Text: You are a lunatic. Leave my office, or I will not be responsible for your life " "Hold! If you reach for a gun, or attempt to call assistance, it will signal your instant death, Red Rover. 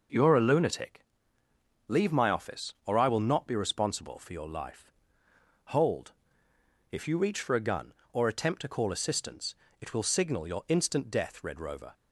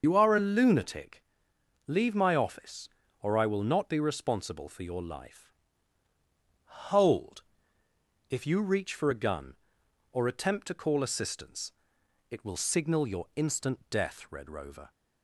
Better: first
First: none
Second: loses the start of "You"; at 0.0 s; 60 ms // starts louder than the rest; until 1.0 s; 6.5 dB

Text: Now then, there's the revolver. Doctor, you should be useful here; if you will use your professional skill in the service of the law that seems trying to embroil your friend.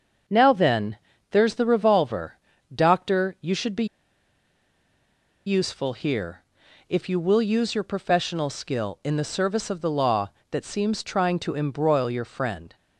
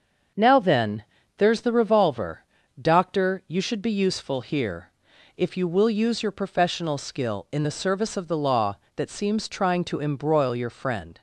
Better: second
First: starts louder than the rest; until 1.6 s; 6.5 dB // pauses between "be" and "useful"; strong; at 3.8 s; 1.6 s long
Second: starts louder than the rest; until 1.7 s; 6.5 dB

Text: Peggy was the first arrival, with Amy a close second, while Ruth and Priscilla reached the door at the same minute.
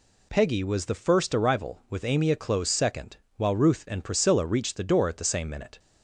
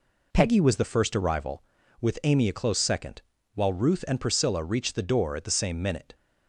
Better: neither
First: none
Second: none

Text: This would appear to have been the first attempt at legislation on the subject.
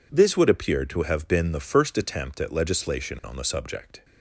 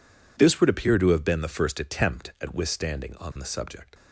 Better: first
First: none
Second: says "withstanding" for "legislation"; at 2.5 s

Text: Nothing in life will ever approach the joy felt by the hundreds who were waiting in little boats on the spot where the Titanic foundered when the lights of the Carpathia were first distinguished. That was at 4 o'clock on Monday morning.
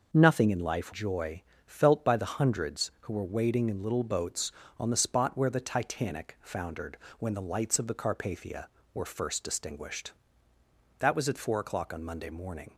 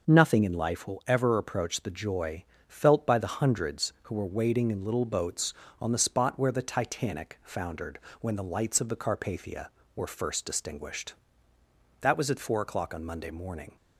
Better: second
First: skips "will ever approach the"; at 0.9 s // pauses between "joy" and "felt"; slight; at 1.4 s; 0.24 s long // pauses between "foundered" and "when"; slight; at 6.9 s; 0.24 s long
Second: pauses between "joy" and "felt"; slight; at 2.4 s; 0.24 s long // pauses between "foundered" and "when"; slight; at 7.9 s; 0.24 s long

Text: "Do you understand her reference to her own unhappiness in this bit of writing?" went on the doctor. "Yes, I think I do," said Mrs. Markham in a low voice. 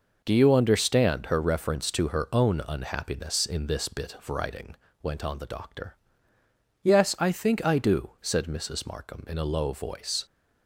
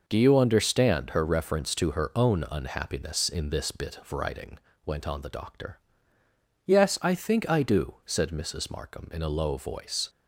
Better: neither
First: none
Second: none

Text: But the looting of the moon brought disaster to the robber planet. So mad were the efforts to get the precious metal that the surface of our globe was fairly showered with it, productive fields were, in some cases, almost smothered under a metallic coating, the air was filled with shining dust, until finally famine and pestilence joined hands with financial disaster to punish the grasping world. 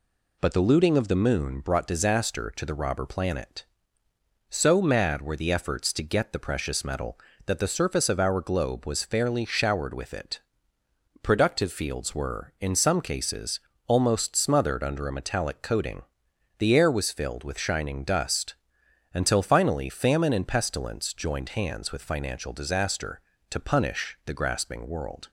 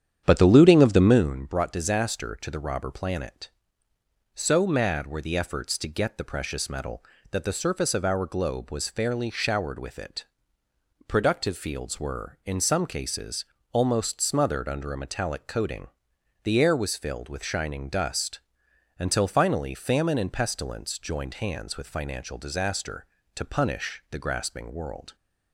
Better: first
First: none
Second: starts louder than the rest; strong; until 1.4 s; 9 dB

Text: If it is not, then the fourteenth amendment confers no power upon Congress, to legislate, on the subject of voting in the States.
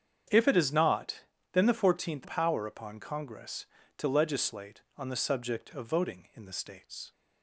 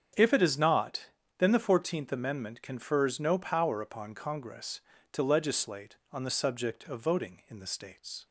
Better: second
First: starts louder than the rest; strong; until 1.6 s; 8 dB // skips "amendment confers no"; at 2.2 s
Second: starts louder than the rest; strong; until 1.4 s; 7.5 dB

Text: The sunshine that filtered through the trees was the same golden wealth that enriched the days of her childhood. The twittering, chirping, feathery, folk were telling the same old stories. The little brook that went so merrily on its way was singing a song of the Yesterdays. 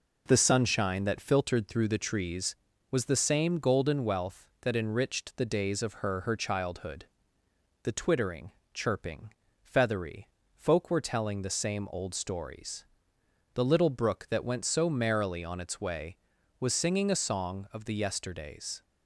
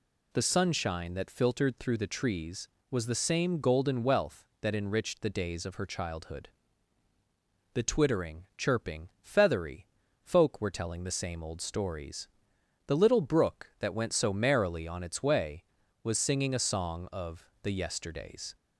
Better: second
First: says "her" twice; at 6.2 s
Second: none

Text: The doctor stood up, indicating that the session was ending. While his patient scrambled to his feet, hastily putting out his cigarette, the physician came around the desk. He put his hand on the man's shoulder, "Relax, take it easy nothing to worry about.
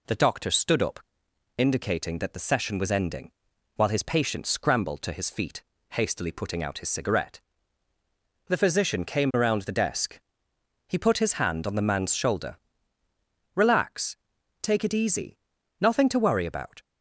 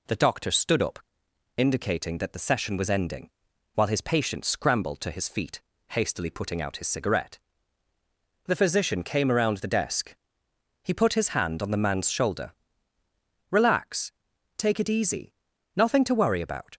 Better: neither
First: pauses between "easy" and "nothing"; at 15.3 s; 0.42 s long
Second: pauses between "easy" and "nothing"; at 15.3 s; 0.42 s long

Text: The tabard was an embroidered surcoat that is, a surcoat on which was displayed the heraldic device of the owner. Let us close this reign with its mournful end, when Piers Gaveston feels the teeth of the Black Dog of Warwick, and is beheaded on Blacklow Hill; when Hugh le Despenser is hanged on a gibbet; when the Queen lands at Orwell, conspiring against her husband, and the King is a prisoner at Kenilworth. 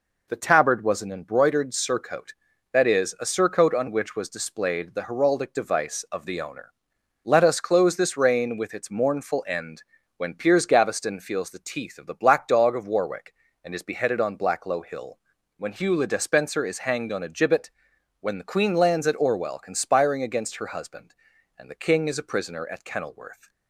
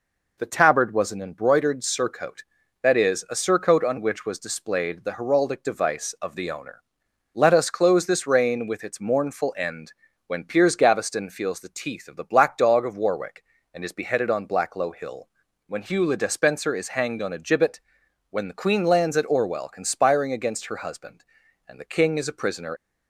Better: first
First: none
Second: stops before "at Kenilworth"; at 22.7 s

